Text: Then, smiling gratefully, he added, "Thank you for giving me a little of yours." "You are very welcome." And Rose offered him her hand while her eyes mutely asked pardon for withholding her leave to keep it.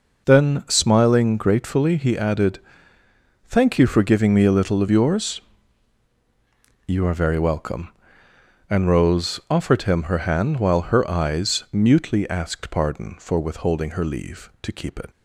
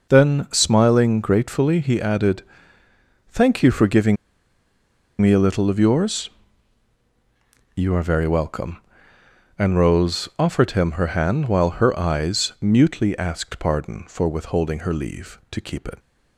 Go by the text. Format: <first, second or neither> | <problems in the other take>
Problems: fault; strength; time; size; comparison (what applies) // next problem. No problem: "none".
first | pauses between "giving" and "me"; at 4.1 s; 1.0 s long